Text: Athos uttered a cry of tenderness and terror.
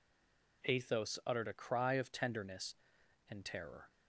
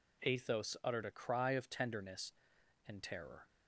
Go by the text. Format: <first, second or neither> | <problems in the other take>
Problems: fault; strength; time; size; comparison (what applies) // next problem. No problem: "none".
second | stays silent before the first word; slight; until 0.6 s; 0.6 s long